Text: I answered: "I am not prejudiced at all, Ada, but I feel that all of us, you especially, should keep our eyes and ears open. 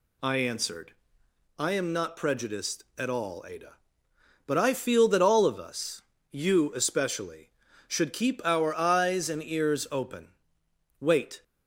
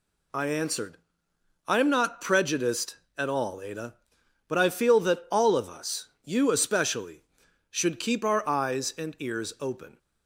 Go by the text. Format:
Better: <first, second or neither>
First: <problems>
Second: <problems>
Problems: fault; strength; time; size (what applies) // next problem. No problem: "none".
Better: second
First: goes on to say "Wait"; slight; from 10.9 s on; 0.44 s long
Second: none